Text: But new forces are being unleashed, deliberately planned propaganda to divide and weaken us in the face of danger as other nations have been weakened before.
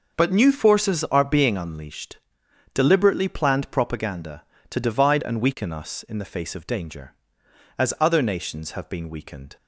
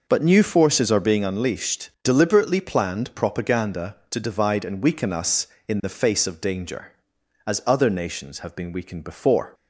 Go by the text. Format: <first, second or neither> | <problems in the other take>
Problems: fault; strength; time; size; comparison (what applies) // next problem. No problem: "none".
second | starts louder than the rest; until 1.2 s; 6 dB // stops before "before"; at 9.5 s